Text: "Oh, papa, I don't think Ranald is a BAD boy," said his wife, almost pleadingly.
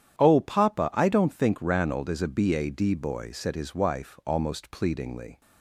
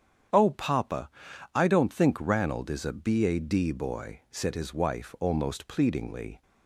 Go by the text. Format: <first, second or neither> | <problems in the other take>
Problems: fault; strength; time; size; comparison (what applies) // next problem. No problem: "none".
neither | starts louder than the rest; strong; the same in both